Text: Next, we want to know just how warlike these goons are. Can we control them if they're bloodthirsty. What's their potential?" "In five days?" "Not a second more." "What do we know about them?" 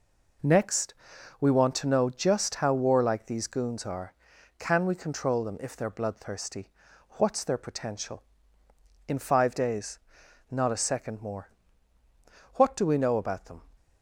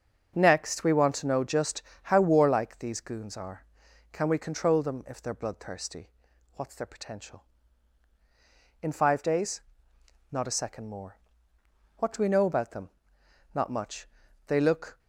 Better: first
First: none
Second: starts louder than the rest; until 1.3 s; 6.5 dB // pauses between "just" and "how"; slight; at 1.8 s; 0.24 s long // goes on to say "Not much They look"; from 13.5 s on; 1.4 s long

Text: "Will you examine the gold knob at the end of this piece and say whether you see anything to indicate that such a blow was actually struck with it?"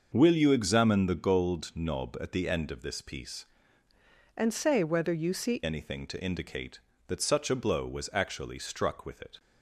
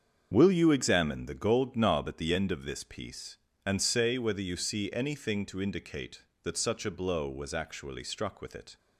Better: second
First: starts louder than the rest; until 1.1 s; 6 dB // changes voice from "and" to "see"; from 4.3 to 5.6 s; 1.3 s long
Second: starts louder than the rest; until 1.3 s; 7 dB

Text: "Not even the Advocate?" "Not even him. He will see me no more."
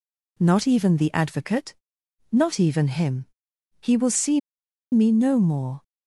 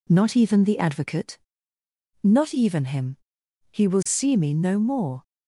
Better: second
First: pauses between "see" and "me"; noticeable; at 4.3 s; 0.52 s long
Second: none

